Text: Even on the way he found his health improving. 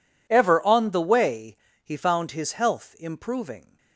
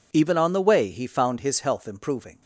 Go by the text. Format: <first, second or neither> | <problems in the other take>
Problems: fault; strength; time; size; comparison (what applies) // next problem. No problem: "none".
second | says "Ever" for "Even"; at 0.2 s // pauses between "way" and "he"; slight; at 1.5 s; 0.28 s long